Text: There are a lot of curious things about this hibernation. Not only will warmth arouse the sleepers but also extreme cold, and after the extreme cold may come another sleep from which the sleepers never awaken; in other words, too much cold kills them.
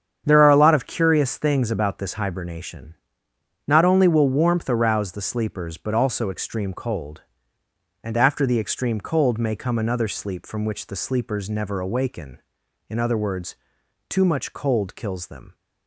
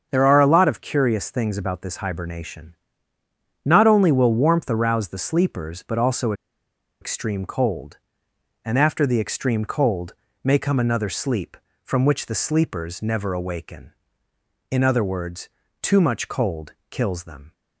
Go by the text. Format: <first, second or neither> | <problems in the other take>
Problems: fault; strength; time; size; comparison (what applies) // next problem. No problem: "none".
first | starts louder than the rest; until 1.1 s; 7 dB; strong in the first // pauses between "also" and "extreme"; noticeable; at 6.3 s; 0.68 s long // pauses between "cold" and "may"; slight; at 10.1 s; 0.28 s long // pauses between "cold" and "kills"; slight; at 16.7 s; 0.18 s long